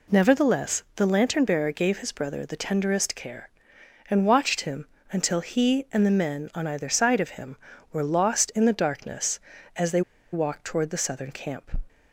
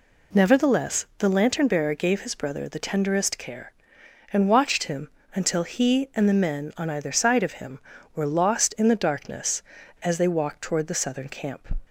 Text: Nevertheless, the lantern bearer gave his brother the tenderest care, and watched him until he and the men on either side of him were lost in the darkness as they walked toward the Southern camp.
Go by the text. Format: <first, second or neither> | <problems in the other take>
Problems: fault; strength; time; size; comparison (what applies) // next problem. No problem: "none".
second | pauses between "him" and "until"; slight; at 4.8 s; 0.24 s long; slight in the second // pauses between "they" and "walked"; slight; at 10.0 s; 0.31 s long